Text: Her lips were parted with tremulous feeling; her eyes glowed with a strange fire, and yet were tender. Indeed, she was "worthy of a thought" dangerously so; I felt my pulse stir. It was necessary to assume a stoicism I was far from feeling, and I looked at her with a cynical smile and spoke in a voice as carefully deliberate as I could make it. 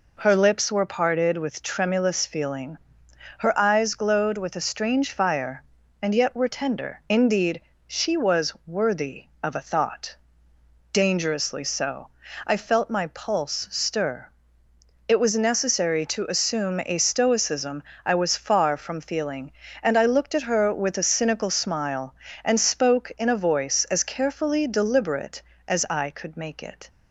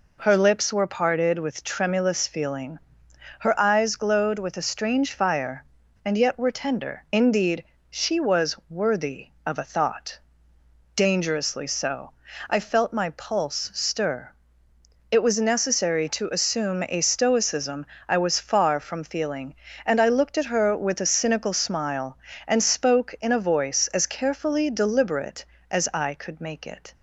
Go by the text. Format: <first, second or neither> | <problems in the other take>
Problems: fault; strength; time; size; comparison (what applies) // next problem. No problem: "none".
neither | pauses between "thought" and "dangerously"; noticeable; the same in both // pauses between "stoicism" and "I"; slight; the same in both